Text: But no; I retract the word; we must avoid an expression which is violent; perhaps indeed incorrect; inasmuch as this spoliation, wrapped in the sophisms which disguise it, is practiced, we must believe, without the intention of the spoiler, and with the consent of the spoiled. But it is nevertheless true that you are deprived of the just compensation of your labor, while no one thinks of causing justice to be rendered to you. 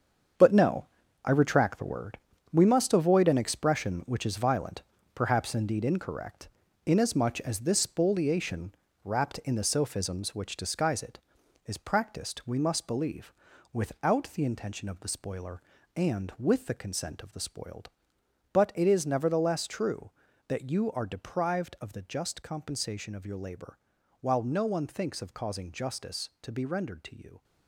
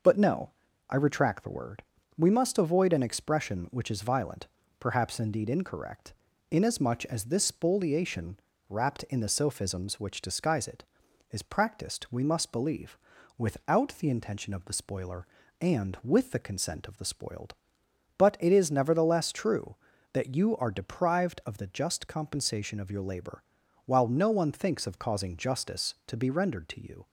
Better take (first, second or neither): second